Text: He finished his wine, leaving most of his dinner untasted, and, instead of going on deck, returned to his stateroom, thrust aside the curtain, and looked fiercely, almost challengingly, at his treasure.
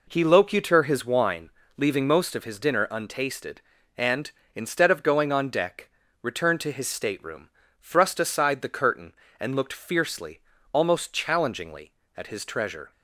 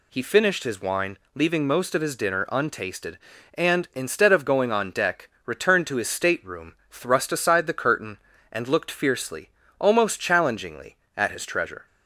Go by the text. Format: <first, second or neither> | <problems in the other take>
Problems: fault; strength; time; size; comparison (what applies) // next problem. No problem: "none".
second | says "locutor" for "finished"; at 0.2 s